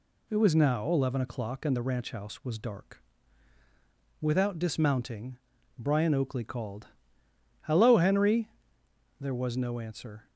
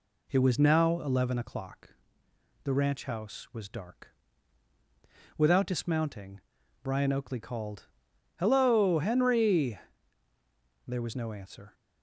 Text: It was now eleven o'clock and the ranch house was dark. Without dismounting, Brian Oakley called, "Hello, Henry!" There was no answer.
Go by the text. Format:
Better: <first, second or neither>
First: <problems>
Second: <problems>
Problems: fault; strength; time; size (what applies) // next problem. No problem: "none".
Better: first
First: none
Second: skips "and"; at 2.2 s